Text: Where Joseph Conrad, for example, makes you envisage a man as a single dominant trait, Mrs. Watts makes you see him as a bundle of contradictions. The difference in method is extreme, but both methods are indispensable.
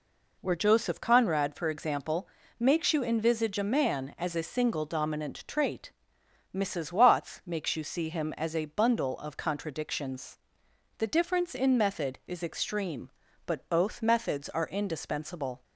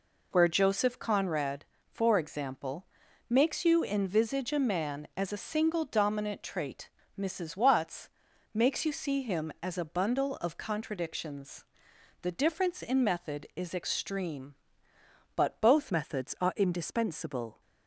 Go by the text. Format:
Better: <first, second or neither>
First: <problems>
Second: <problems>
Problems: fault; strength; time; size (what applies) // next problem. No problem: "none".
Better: first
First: none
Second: pauses between "Watts" and "makes"; noticeable; at 8.0 s; 0.46 s long // changes voice at "methods"; from 15.9 s on; 1.7 s long